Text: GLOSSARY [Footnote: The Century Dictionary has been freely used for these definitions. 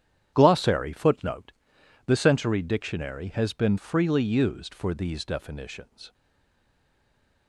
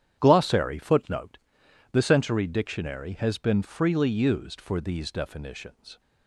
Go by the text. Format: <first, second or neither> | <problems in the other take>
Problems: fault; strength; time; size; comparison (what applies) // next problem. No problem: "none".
second | starts louder than the rest; strong; until 1.3 s; 10 dB; strong in the second // stays silent after the last word; noticeable; from 6.1 s on; 1.3 s long